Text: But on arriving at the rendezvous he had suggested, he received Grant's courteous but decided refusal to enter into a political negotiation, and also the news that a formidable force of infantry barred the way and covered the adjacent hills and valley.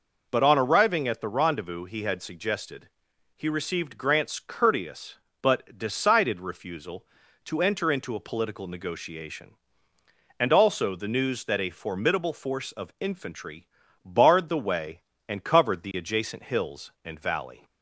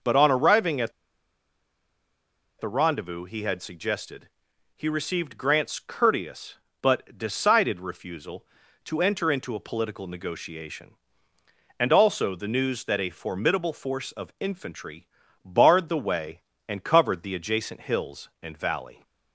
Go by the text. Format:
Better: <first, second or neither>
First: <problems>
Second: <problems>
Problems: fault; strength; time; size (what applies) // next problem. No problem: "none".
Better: first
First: pauses between "infantry" and "barred"; at 13.6 s; 0.38 s long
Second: pauses between "at" and "the"; strong; at 0.9 s; 1.6 s long // pauses between "infantry" and "barred"; at 15.0 s; 0.38 s long